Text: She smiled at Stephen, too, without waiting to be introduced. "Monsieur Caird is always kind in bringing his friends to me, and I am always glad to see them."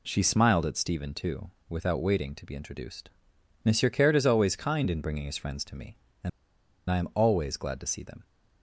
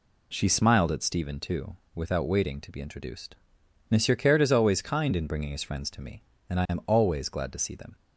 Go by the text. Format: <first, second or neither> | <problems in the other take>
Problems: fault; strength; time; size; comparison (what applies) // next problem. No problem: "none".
second | pauses between "and" and "I"; noticeable; at 6.2 s; 0.59 s long